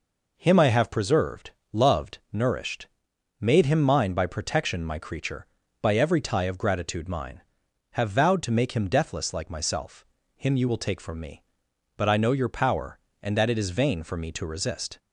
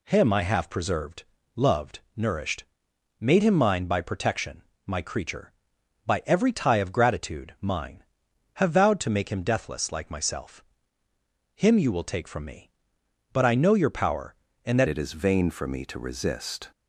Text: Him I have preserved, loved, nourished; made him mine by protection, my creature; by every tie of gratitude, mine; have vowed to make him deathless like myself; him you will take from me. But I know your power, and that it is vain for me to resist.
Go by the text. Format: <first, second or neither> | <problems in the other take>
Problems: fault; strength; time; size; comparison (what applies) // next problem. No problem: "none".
first | changes voice at "it"; from 14.8 s on; 1.9 s long